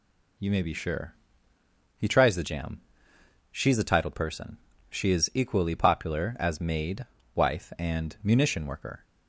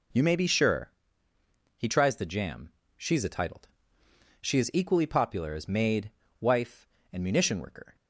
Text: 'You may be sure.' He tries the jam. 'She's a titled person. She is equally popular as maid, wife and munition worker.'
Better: first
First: none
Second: skips "person"; at 4.0 s

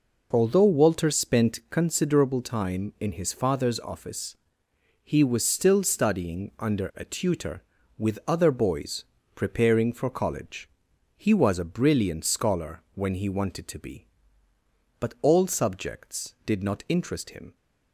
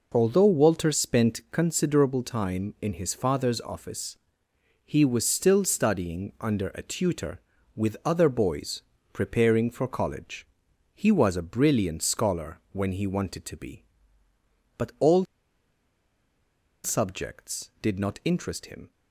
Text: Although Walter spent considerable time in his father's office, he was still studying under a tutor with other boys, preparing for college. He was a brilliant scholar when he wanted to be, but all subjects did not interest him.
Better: first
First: none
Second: pauses between "all" and "subjects"; strong; at 15.2 s; 1.5 s long

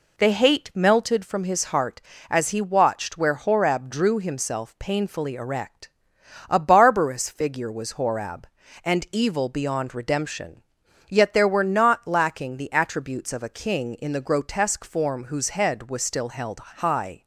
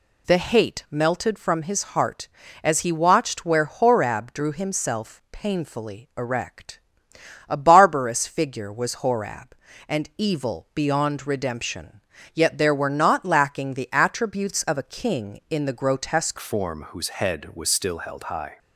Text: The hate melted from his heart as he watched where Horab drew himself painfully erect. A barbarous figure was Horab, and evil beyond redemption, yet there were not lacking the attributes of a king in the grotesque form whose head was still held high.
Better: first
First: none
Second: changes voice at "form"; from 16.4 s on; 2.1 s long

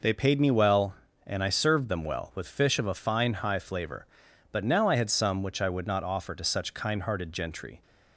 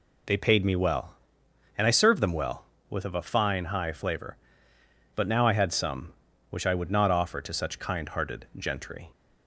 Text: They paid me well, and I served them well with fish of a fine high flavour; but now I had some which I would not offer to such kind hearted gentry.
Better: first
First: none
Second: skips "fish"; at 3.0 s

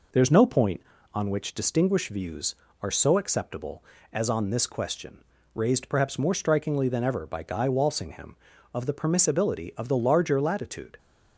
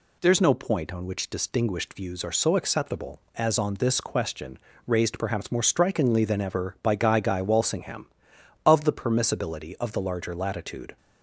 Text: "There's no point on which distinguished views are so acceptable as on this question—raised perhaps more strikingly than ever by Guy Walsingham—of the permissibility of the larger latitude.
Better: first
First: none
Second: says "Guy" twice; at 7.2 s

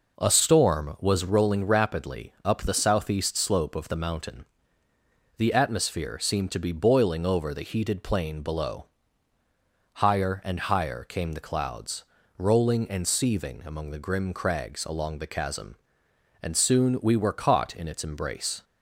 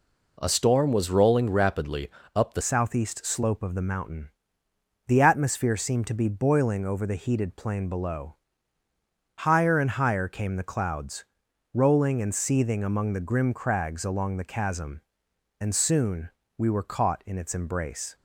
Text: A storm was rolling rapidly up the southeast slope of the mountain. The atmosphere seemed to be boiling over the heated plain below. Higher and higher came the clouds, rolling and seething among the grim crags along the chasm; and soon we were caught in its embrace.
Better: first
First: none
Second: pauses between "rapidly" and "up"; slight; at 2.0 s; 0.24 s long // changes voice at "southeast"; from 2.6 s on; 15.5 s long // pauses between "soon" and "we"; slight; at 16.3 s; 0.26 s long

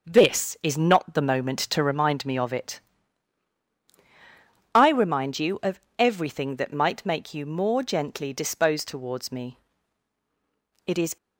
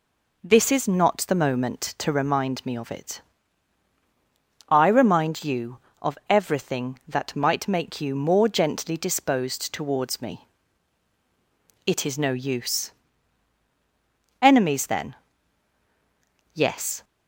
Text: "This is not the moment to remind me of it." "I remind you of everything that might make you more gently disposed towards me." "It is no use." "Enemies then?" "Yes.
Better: second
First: starts louder than the rest; until 1.1 s; 6.5 dB // pauses between "of" and "everything"; slight; at 5.7 s; 0.20 s long // stops before "no use Enemies then Yes"; at 11.1 s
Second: none

